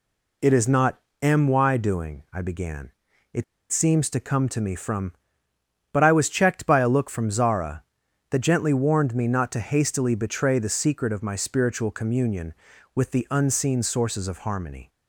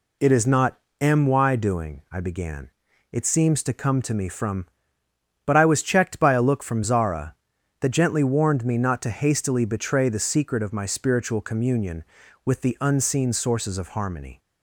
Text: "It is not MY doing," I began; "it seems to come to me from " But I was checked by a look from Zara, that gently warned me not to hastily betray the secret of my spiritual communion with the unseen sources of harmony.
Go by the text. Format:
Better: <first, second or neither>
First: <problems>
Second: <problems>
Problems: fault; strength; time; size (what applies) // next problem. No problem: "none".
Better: second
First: pauses between "not" and "MY"; slight; at 0.9 s; 0.22 s long // pauses between "it" and "seems"; slight; at 3.4 s; 0.28 s long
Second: pauses between "not" and "MY"; slight; at 0.7 s; 0.22 s long